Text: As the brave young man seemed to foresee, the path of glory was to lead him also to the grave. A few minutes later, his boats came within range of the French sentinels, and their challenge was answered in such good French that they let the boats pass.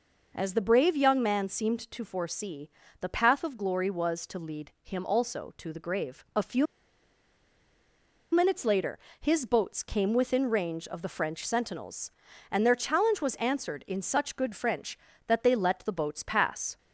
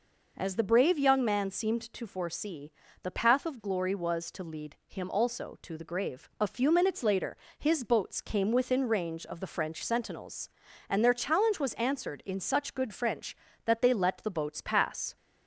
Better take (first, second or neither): second